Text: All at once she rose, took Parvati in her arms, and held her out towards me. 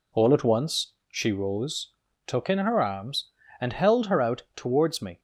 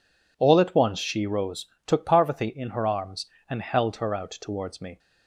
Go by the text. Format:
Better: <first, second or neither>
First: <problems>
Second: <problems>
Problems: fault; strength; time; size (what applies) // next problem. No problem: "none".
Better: second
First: pauses between "once" and "she"; slight; at 0.9 s; 0.16 s long // skips "Parvati"; at 2.5 s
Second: none